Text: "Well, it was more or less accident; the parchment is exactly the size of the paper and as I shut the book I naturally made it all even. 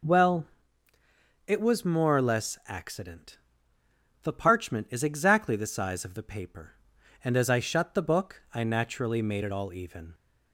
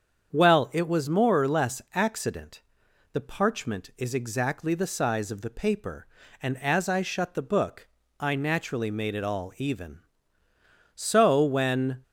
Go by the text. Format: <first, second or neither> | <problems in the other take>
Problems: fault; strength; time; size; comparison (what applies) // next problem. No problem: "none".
first | starts louder than the rest; strong; until 1.3 s; 7.5 dB // pauses between "book" and "I"; slight; at 7.8 s; 0.32 s long // goes on to say "So when"; noticeable; from 10.9 s on; 1.0 s long